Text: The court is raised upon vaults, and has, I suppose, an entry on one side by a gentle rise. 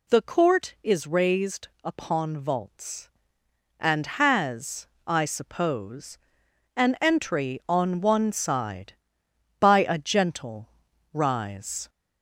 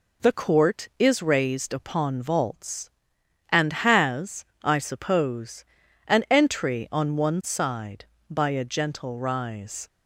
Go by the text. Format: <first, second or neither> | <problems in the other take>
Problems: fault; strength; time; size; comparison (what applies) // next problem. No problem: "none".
second | gets louder; slight; throughout; 2 dB // pauses between "raised" and "upon"; slight; at 1.6 s; 0.16 s long // pauses between "gentle" and "rise"; at 10.6 s; 0.42 s long